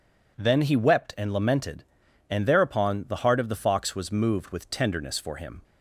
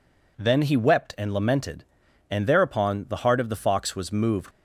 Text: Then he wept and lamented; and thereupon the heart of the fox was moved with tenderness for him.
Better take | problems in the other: first | stops before "with tenderness for him"; at 4.5 s

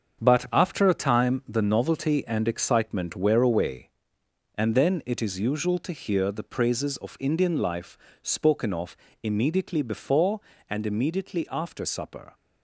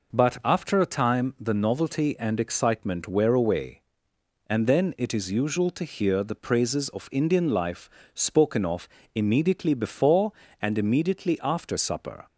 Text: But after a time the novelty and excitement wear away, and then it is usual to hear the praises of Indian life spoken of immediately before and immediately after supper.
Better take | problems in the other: second | gets quieter; strong; throughout; 8 dB // pauses between "life" and "spoken"; slight; at 7.9 s; 0.24 s long; slight in the second // pauses between "of" and "immediately"; slight; at 8.9 s; 0.26 s long; slight in the second

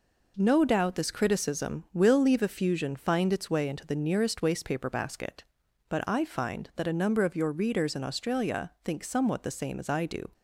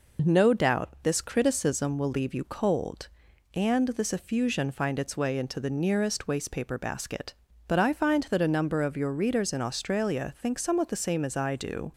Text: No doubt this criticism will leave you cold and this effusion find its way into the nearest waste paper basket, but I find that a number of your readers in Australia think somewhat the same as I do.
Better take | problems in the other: second | skips "you cold and this"; at 2.4 s

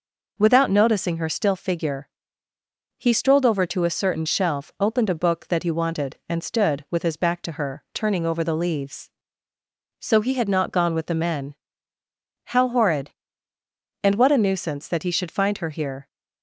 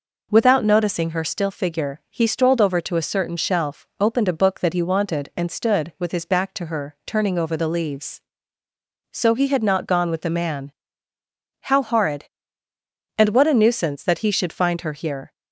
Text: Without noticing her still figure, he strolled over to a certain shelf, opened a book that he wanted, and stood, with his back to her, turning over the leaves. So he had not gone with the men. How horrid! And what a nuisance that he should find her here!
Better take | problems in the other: first | says "man" for "men"; at 10.2 s

